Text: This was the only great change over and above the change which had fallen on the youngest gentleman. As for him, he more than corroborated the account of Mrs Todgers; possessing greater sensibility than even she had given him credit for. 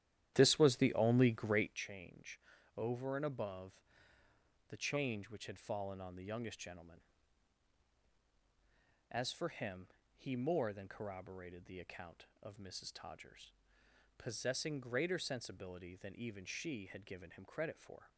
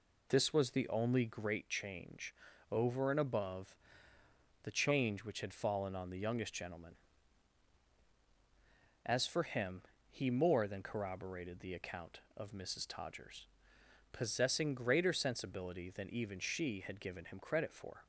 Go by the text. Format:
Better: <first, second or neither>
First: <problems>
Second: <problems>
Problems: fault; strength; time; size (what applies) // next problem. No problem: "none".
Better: second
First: starts louder than the rest; strong; until 1.8 s; 11.5 dB // pauses between "change" and "over"; slight; at 2.3 s; 0.36 s long // pauses between "above" and "the"; noticeable; at 3.7 s; 0.90 s long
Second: pauses between "change" and "over"; slight; at 2.3 s; 0.36 s long // pauses between "above" and "the"; noticeable; at 3.7 s; 0.90 s long